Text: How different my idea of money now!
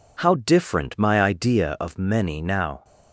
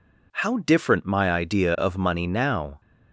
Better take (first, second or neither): second